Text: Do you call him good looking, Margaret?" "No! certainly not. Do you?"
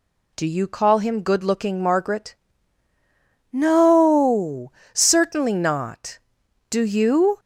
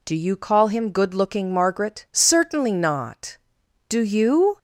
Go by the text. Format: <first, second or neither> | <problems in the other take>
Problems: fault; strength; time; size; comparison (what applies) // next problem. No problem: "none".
first | skips "No"; at 2.1 s